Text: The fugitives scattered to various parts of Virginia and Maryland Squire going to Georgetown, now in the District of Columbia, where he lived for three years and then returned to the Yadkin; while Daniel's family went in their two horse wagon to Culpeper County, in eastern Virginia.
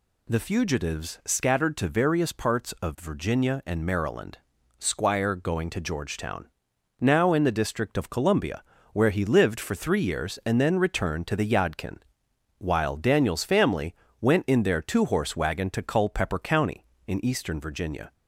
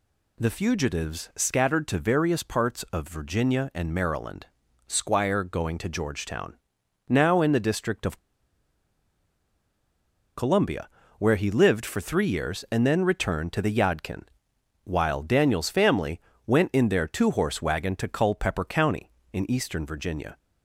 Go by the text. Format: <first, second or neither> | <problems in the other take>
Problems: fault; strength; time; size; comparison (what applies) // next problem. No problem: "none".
first | pauses between "Maryland" and "Squire"; at 4.4 s; 0.38 s long; also in the first // pauses between "of" and "Columbia"; strong; at 8.1 s; 2.1 s long // pauses between "family" and "went"; slight; at 16.2 s; 0.24 s long; slight in the first